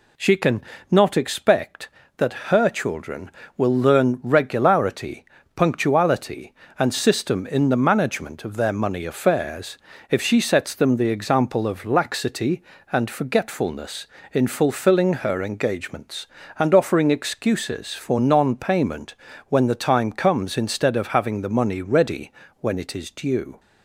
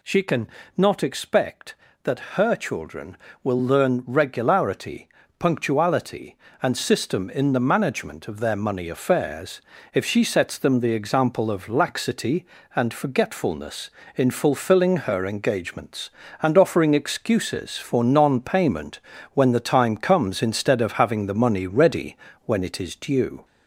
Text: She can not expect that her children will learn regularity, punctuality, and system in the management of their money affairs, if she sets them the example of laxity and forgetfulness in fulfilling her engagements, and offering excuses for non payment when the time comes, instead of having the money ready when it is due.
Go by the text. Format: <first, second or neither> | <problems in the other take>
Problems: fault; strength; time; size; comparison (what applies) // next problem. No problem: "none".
first | gets louder; slight; throughout; 2 dB // pauses between "can" and "not"; slight; at 0.4 s; 0.28 s long; slight in the first // pauses between "payment" and "when"; slight; at 19.0 s; 0.32 s long; slight in the first // pauses between "ready" and "when"; slight; at 22.1 s; 0.28 s long; slight in the first